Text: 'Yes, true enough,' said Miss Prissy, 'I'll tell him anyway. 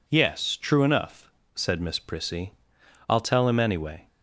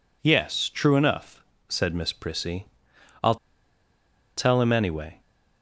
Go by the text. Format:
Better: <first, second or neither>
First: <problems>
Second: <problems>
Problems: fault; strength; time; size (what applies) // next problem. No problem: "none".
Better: first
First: none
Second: pauses between "I'll" and "tell"; at 3.3 s; 1.0 s long